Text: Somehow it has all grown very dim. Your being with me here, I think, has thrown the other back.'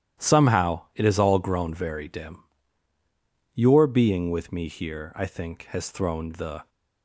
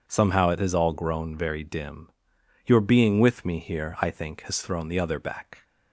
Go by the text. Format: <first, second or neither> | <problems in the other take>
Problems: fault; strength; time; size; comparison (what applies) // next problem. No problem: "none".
second | starts louder than the rest; strong; until 1.3 s; 12.5 dB // pauses between "Somehow" and "it"; slight; at 0.8 s; 0.16 s long // stops before "other back"; at 6.6 s